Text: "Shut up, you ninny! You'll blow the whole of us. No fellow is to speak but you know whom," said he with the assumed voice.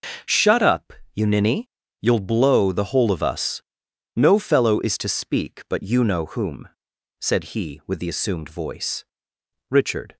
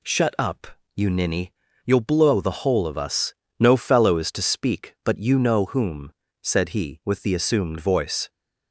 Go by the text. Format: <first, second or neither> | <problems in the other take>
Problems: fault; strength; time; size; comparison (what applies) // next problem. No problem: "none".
second | starts louder than the rest; until 1.4 s; 6.5 dB // goes on to say "Richard"; slight; from 9.7 s on; 0.46 s long